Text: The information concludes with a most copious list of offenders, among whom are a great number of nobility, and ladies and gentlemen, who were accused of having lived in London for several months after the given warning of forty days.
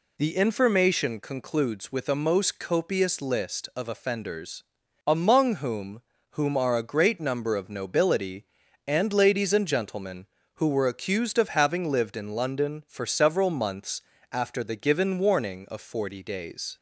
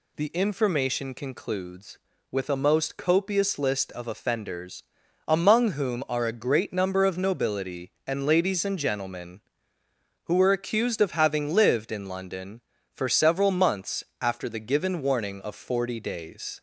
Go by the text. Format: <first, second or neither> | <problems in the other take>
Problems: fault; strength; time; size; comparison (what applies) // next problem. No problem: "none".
second | says "whom" twice; at 6.3 s // pauses between "months" and "after"; slight; at 14.0 s; 0.30 s long; slight in the second